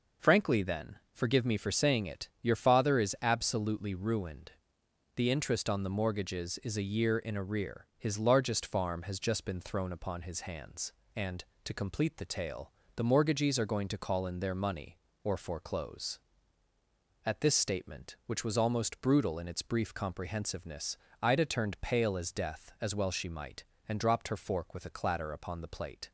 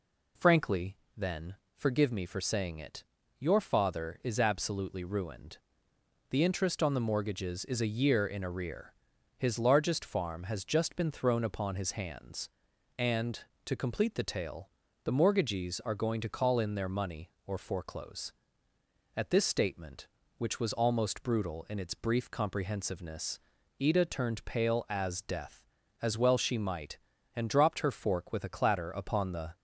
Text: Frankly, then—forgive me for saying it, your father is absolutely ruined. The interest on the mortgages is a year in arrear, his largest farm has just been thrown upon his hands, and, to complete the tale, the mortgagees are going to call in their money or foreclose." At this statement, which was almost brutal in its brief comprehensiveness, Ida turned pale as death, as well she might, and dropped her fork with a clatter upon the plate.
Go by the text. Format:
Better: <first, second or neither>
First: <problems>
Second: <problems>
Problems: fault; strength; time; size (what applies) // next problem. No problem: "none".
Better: first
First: none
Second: stops before "plate"; at 29.5 s